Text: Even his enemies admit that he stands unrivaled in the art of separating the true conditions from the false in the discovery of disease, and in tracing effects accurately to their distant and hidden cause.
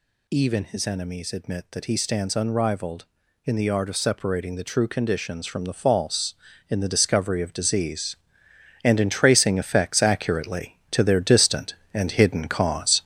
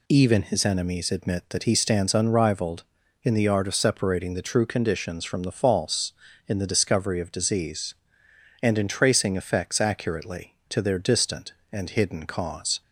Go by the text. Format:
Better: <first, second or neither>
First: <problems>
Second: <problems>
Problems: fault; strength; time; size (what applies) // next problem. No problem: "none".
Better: second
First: gets louder; throughout; 6.5 dB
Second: none